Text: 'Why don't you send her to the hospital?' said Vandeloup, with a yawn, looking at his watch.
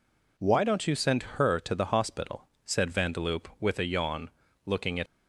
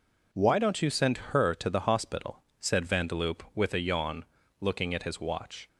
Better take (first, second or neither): second